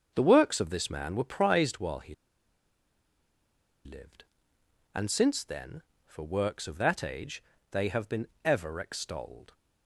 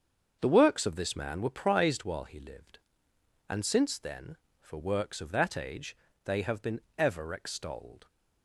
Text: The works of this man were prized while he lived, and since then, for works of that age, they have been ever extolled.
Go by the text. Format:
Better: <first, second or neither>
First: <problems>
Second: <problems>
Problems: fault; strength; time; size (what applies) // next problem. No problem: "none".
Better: second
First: starts louder than the rest; until 1.1 s; 7 dB // pauses between "he" and "lived"; strong; at 2.1 s; 1.7 s long // pauses between "been" and "ever"; slight; at 8.2 s; 0.18 s long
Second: starts louder than the rest; until 1.4 s; 6.5 dB // pauses between "been" and "ever"; slight; at 6.8 s; 0.18 s long